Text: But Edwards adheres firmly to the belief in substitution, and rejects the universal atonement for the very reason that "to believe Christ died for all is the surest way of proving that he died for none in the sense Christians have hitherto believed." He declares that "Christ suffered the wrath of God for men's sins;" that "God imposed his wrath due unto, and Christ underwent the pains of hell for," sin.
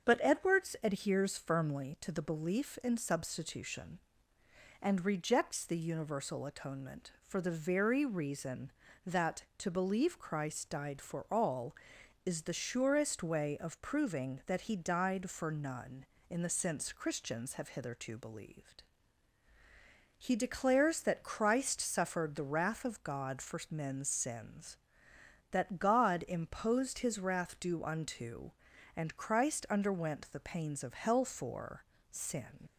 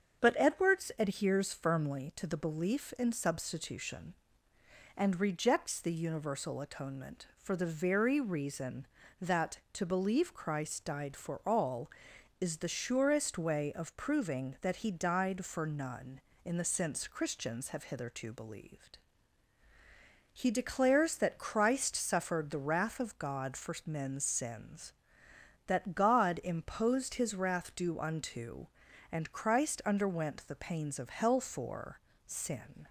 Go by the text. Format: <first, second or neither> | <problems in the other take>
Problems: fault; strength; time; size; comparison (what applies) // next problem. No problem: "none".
second | starts louder than the rest; strong; until 1.1 s; 7.5 dB; strong in the second // leaves "sin" unfinished; at 32.6 s; 60 ms